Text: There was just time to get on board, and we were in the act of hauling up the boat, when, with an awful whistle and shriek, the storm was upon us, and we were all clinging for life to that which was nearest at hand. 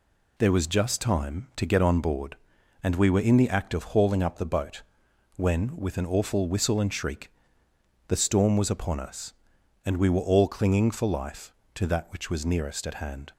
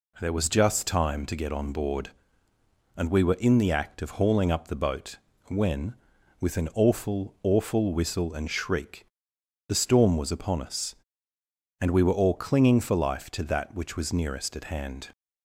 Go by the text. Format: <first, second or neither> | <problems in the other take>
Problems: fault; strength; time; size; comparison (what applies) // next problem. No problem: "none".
first | says "awful" twice; at 7.4 s